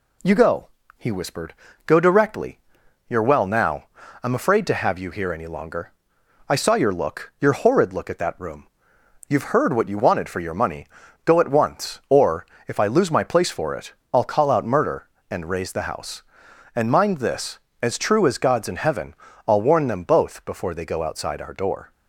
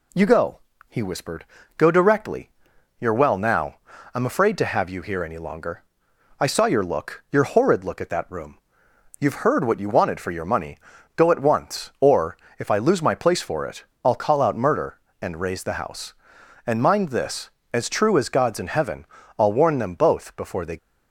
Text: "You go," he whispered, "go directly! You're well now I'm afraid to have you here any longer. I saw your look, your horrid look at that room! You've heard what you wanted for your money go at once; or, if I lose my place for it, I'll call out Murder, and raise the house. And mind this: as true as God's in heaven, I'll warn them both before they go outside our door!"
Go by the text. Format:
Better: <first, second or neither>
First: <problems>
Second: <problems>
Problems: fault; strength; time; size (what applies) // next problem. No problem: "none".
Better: first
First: pauses between "now" and "I'm"; at 3.8 s; 0.38 s long // pauses between "money" and "go"; slight; at 10.8 s; 0.36 s long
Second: pauses between "now" and "I'm"; at 3.7 s; 0.38 s long // pauses between "money" and "go"; slight; at 10.7 s; 0.36 s long // stops before "go outside our door"; at 20.7 s